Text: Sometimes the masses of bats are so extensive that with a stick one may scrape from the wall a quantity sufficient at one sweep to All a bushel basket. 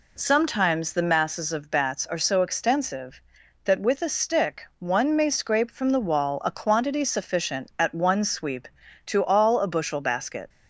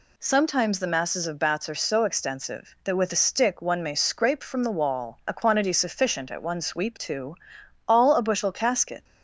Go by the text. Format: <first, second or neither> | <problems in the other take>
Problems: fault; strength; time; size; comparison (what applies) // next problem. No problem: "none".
first | pauses between "to" and "All"; noticeable; at 7.3 s; 0.50 s long // says "casket" for "basket"; at 8.5 s